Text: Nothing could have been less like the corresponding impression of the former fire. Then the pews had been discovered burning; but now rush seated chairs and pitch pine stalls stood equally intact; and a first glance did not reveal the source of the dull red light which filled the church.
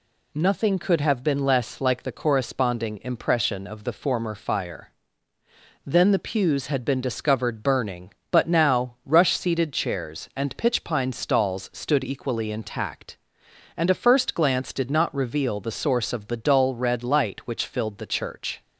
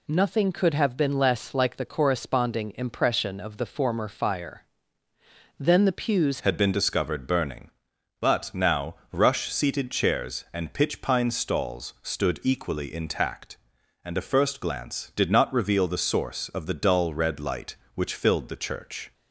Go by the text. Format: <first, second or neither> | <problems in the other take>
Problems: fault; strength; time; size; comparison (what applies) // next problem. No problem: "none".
first | changes voice at "had"; from 6.4 s on; 12.7 s long // pauses between "now" and "rush"; slight; at 8.9 s; 0.18 s long